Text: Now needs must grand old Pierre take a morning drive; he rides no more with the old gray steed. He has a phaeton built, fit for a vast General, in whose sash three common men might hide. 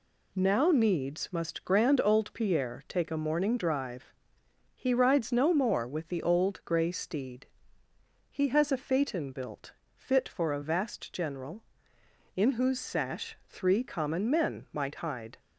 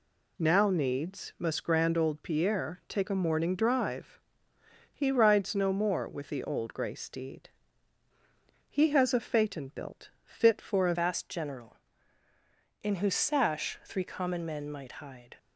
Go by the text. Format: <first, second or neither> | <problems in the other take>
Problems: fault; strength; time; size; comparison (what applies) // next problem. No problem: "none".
first | changes voice at "vast"; from 10.9 s on; 4.4 s long